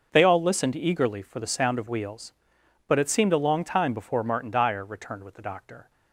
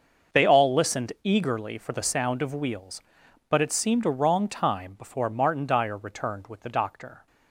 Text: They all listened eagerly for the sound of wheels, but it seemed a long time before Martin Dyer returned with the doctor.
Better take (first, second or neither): first